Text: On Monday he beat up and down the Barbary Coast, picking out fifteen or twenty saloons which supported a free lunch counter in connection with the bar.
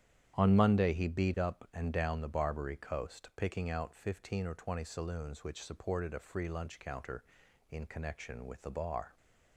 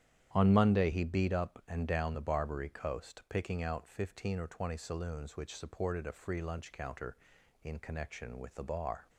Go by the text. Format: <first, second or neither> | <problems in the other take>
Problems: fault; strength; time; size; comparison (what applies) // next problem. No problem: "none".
neither | starts louder than the rest; strong; the same in both